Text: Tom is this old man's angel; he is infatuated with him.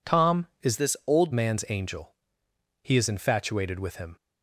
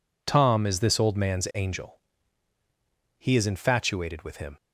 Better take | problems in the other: second | changes voice from "this" to "old"; from 0.7 to 1.3 s; 0.6 s long

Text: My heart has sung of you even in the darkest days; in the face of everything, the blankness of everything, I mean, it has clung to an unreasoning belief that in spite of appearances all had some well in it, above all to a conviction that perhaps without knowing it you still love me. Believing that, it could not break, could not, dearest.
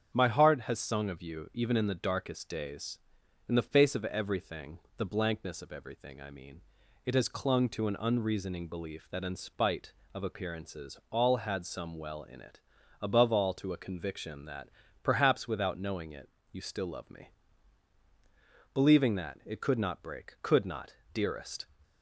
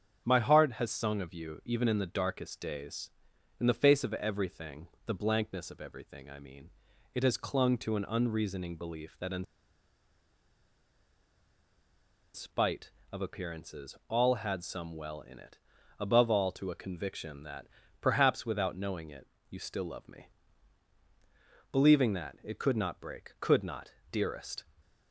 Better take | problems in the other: first | starts louder than the rest; strong; until 1.2 s; 7.5 dB; strong in the first // pauses between "in" and "spite"; strong; at 9.4 s; 2.9 s long // pauses between "that" and "perhaps"; slight; at 17.6 s; 0.34 s long; slight in the first // pauses between "it" and "you"; slight; at 19.2 s; 0.24 s long; slight in the first

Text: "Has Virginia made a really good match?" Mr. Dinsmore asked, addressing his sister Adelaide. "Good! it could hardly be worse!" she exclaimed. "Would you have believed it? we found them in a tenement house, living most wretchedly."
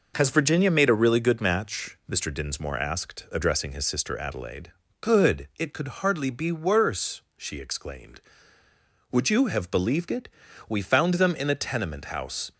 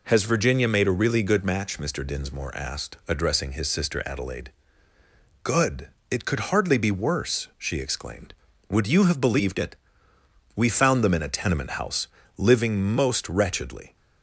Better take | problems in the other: second | stops before "living most wretchedly"; at 12.5 s

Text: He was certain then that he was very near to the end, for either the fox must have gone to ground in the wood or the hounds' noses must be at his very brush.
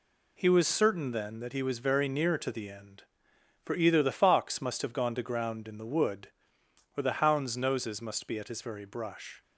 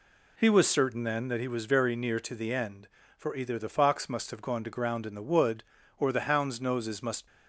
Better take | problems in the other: first | stops before "be at his very brush"; at 7.2 s

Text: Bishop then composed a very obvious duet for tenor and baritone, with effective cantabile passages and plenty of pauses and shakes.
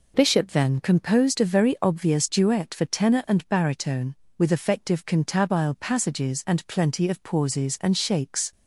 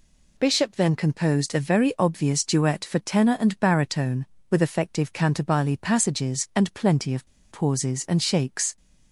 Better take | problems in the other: first | pauses between "of" and "pauses"; slight; at 7.2 s; 0.23 s long

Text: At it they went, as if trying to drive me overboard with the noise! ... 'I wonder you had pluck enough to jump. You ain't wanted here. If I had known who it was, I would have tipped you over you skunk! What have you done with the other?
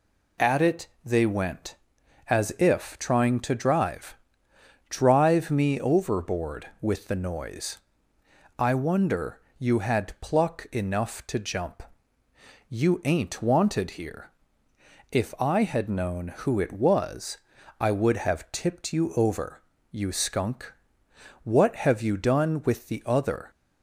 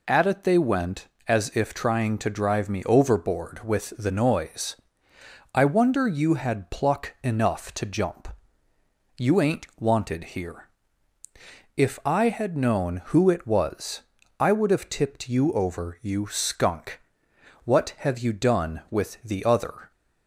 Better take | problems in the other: second | pauses between "it" and "they"; slight; at 0.8 s; 0.16 s long // says "drive" twice; at 4.8 s // pauses between "wonder" and "you"; slight; at 9.3 s; 0.20 s long // pauses between "over" and "you"; slight; at 19.5 s; 0.30 s long

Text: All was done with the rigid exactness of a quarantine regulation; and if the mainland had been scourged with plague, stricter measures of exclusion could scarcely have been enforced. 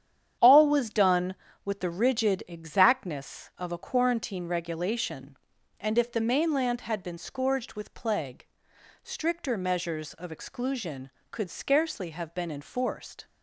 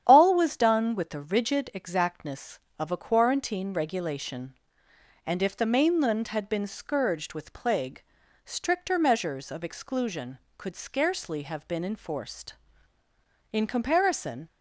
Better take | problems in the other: first | starts louder than the rest; strong; until 1.0 s; 9.5 dB; strong in the first // goes on to say "In comparison"; noticeable; from 13.5 s on; 0.96 s long

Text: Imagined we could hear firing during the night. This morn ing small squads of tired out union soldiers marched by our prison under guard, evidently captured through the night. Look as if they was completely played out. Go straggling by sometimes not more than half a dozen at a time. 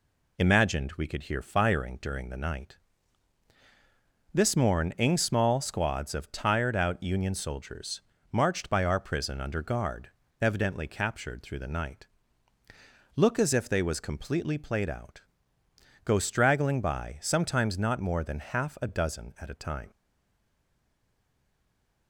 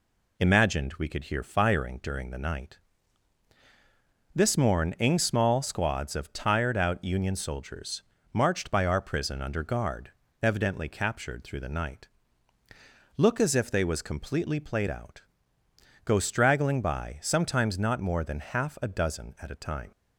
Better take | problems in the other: second | pauses between "soldiers" and "marched"; slight; at 8.0 s; 0.30 s long; slight in the second // stays silent after the last word; from 19.9 s on; 2.1 s long

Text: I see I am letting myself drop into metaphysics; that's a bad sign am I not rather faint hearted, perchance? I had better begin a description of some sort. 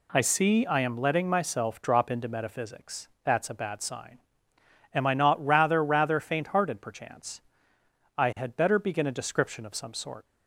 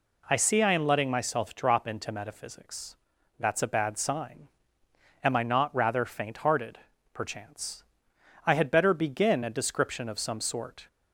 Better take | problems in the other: second | pauses between "sign" and "am"; noticeable; at 4.1 s; 0.74 s long; noticeable in the second // says "rather" twice; at 5.8 s

